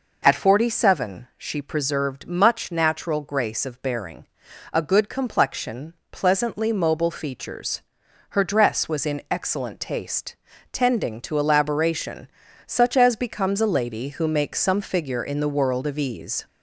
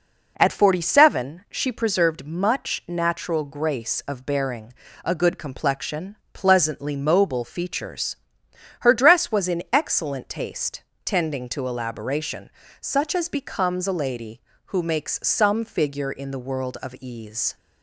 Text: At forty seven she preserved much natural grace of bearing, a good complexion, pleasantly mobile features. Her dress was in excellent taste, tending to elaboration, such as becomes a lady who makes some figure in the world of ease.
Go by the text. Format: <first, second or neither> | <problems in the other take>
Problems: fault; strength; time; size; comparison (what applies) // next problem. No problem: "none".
second | gets louder; slight; throughout; 2 dB